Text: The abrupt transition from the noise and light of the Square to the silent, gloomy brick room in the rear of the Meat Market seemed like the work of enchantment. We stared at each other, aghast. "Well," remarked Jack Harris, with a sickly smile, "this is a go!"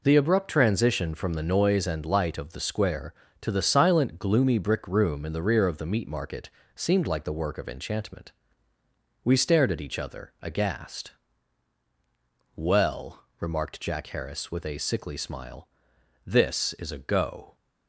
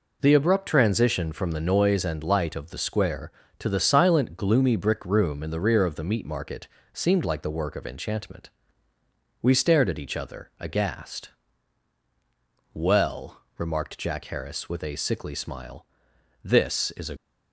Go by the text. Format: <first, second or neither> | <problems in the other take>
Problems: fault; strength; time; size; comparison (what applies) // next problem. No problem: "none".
first | pauses between "Market" and "seemed"; slight; at 6.6 s; 0.26 s long; slight in the first // stops before "go"; at 17.1 s